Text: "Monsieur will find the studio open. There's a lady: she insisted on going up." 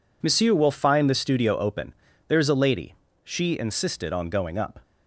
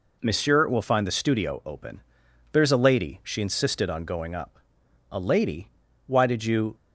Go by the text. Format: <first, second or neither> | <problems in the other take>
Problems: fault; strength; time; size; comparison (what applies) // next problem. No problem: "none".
first | goes on to say "A lady Why did you"; from 5.0 s on; 1.6 s long